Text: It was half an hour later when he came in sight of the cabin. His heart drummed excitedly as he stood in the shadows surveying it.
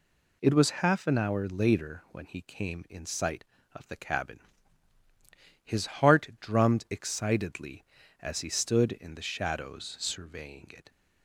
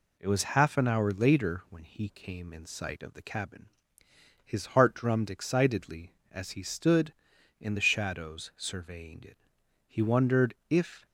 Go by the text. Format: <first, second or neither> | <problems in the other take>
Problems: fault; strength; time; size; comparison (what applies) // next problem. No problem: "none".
first | goes on to say "He wondered if"; noticeable; from 9.8 s on; 1.1 s long